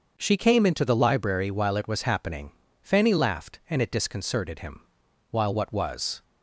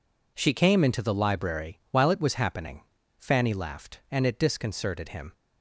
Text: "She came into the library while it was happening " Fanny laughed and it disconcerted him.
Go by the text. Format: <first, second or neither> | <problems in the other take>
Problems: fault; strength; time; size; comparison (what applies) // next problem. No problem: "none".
second | starts louder than the rest; until 1.1 s; 6.5 dB // goes on to say "While what was"; noticeable; from 5.2 s on; 0.94 s long